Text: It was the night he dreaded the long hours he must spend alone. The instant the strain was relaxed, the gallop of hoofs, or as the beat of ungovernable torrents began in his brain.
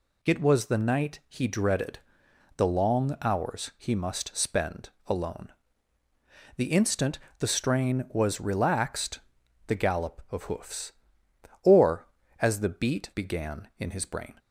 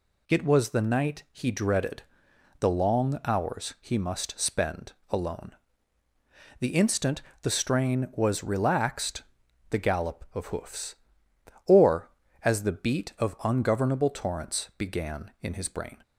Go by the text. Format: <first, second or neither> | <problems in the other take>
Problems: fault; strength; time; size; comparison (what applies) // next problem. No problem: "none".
second | pauses between "dreaded" and "the"; noticeable; at 1.9 s; 0.60 s long; noticeable in the second // pauses between "spend" and "alone"; slight; at 4.8 s; 0.18 s long; slight in the second // pauses between "instant" and "the"; slight; at 7.1 s; 0.22 s long; slight in the second // skips "of ungovernable torrents"; at 13.1 s